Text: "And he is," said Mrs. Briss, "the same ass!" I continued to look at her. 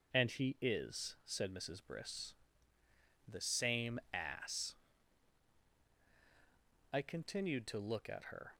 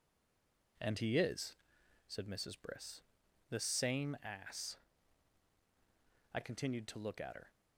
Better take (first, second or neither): first